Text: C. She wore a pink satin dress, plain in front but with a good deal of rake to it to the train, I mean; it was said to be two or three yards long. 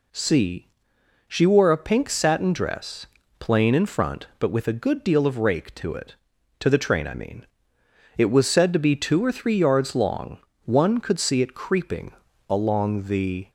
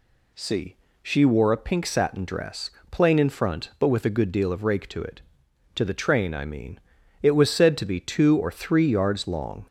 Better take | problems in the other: second | goes on to say "One could see it creeping along the"; strong; from 10.6 s on; 2.8 s long

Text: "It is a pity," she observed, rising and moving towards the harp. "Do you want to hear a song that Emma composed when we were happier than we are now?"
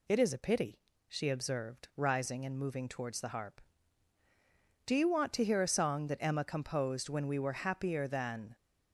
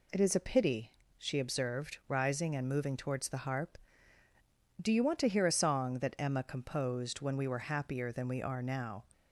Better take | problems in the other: second | stops before "we are now"; at 8.5 s

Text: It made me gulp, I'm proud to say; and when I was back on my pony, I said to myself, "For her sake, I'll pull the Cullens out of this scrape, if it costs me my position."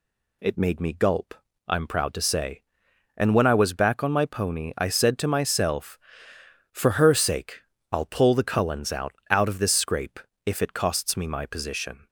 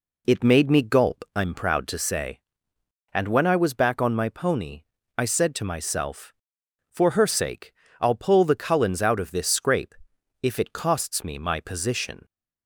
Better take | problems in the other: second | says "out" twice; at 9.2 s

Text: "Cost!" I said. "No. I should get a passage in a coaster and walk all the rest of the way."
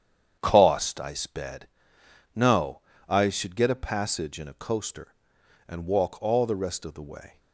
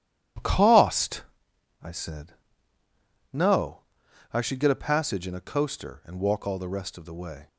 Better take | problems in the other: second | starts louder than the rest; strong; until 1.4 s; 8.5 dB // says "sped" for "said"; at 1.1 s

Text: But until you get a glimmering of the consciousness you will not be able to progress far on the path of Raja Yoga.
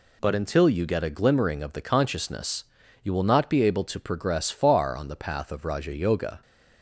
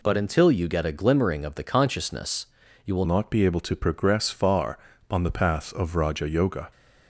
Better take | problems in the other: first | pauses between "consciousness" and "you"; at 2.4 s; 0.38 s long; also in the first // changes voice at "not"; from 3.0 s on; 3.6 s long

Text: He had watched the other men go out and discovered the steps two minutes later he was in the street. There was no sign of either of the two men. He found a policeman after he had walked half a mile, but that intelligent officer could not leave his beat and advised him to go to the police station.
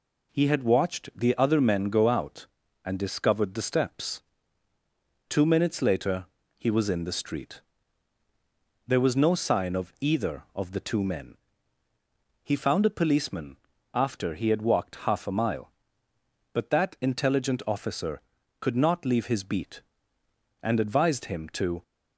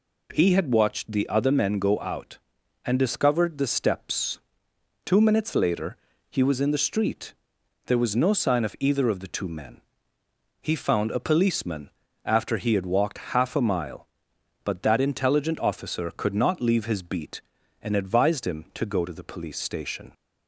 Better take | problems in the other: second | pauses between "steps" and "two"; at 4.2 s; 1.0 s long; noticeable in the second // pauses between "later" and "he"; slight; at 6.2 s; 0.32 s long; slight in the second // pauses between "policeman" and "after"; at 13.5 s; 0.38 s long; slight in the second // stops before "go to the police station"; at 21.8 s

